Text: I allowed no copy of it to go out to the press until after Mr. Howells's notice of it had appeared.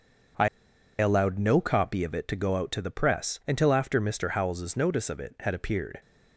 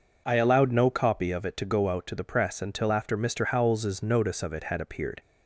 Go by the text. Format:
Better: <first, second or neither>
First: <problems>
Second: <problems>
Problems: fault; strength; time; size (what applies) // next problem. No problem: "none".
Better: second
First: pauses between "I" and "allowed"; noticeable; at 0.4 s; 0.51 s long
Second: none